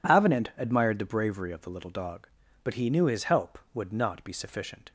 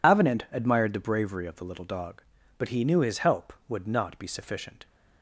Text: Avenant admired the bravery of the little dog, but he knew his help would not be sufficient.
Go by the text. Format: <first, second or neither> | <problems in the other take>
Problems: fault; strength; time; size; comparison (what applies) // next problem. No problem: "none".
first | loses the start of "Avenant"; at 0.0 s; 55 ms